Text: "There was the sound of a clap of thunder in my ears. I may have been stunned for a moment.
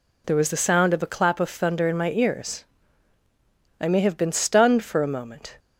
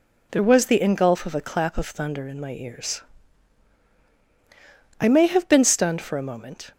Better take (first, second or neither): first